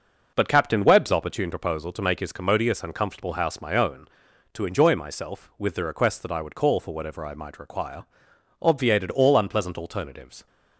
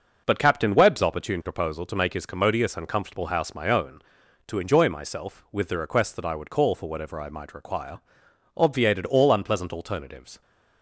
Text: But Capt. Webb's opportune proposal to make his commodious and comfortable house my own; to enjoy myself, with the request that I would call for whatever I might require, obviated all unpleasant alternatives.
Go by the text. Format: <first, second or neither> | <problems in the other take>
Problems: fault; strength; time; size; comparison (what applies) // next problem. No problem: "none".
neither | none